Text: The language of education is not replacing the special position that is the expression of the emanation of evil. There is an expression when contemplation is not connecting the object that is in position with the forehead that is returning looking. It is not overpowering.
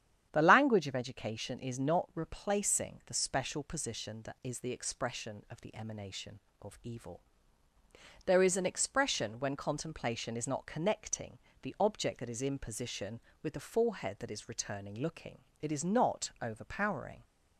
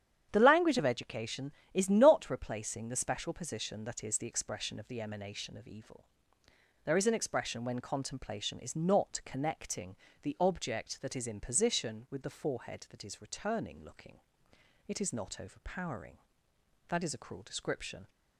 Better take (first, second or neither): first